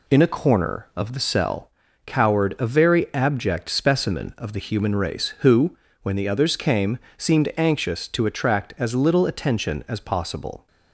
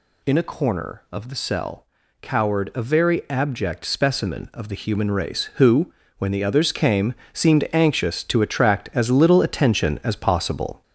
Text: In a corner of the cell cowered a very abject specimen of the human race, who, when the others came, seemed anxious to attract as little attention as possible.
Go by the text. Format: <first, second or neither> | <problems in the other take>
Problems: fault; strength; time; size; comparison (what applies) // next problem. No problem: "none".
first | gets louder; noticeable; throughout; 5.5 dB // pauses between "cell" and "cowered"; slight; at 1.8 s; 0.36 s long; slight in the first